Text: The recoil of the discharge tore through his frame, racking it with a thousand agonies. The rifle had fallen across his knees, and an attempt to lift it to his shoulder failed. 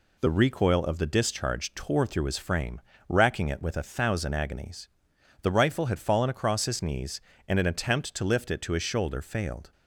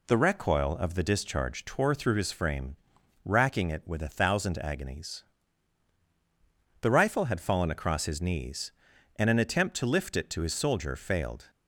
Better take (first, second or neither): first